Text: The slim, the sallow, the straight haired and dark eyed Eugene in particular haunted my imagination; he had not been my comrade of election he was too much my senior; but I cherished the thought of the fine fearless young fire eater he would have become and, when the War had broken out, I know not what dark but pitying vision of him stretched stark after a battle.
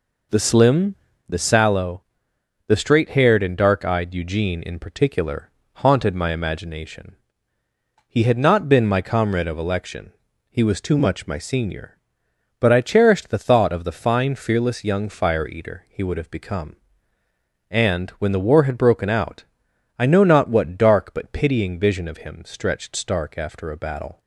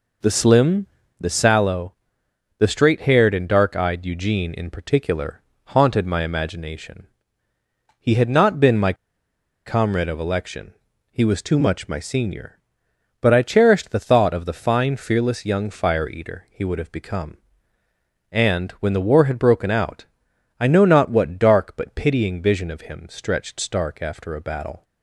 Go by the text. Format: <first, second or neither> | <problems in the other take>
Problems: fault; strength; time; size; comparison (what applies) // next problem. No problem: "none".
first | pauses between "particular" and "haunted"; slight; at 5.4 s; 0.32 s long; slight in the first // pauses between "my" and "comrade"; noticeable; at 8.9 s; 0.72 s long // pauses between "election" and "he"; slight; at 10.7 s; 0.36 s long; slight in the first